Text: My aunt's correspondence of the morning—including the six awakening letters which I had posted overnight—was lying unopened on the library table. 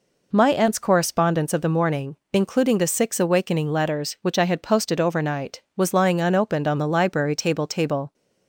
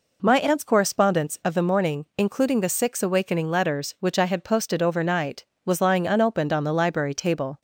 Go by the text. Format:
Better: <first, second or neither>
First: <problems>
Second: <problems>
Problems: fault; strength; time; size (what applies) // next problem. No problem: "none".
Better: second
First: says "table" twice; at 7.6 s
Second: none